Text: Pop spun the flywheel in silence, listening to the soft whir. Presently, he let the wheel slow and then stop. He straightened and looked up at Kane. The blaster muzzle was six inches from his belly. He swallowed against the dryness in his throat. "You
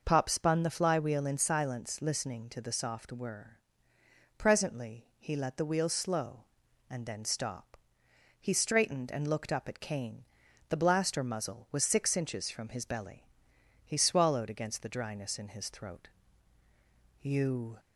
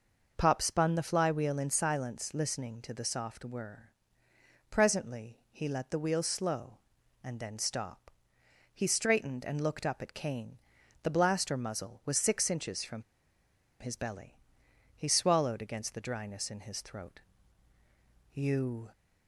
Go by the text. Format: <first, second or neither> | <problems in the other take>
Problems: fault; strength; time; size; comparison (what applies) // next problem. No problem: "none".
first | pauses between "from" and "his"; noticeable; at 13.0 s; 0.78 s long